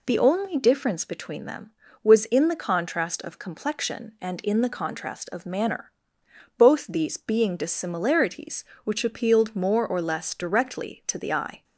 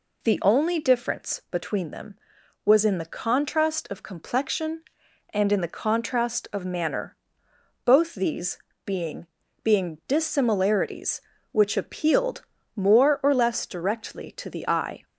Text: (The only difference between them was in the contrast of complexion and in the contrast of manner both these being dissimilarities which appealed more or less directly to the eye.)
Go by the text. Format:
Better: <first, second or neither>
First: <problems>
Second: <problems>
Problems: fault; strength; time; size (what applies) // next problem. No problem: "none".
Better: first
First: pauses between "manner" and "both"; noticeable; at 5.9 s; 0.68 s long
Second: pauses between "manner" and "both"; noticeable; at 7.1 s; 0.70 s long // pauses between "these" and "being"; slight; at 8.5 s; 0.26 s long // says "being" twice; at 9.6 s // pauses between "appealed" and "more"; slight; at 12.4 s; 0.32 s long